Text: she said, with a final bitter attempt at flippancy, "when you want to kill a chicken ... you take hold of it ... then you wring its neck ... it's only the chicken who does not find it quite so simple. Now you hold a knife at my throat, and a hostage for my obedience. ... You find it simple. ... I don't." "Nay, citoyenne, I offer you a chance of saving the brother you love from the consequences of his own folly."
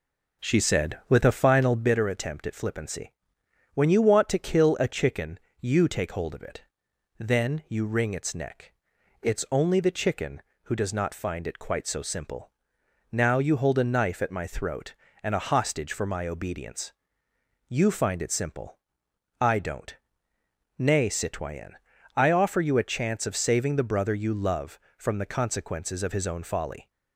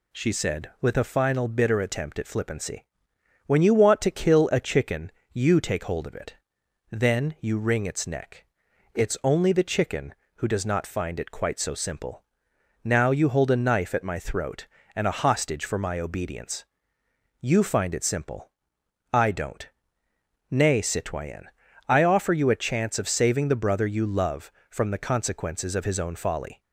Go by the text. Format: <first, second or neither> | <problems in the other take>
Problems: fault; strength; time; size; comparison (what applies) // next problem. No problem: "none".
second | starts louder than the rest; noticeable; until 2.0 s; 4.5 dB